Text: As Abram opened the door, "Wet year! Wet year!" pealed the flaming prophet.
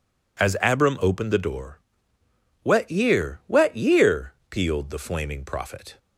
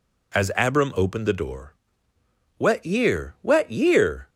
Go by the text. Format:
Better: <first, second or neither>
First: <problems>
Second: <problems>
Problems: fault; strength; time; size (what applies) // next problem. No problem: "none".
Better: first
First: none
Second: stops before "pealed the flaming prophet"; at 4.2 s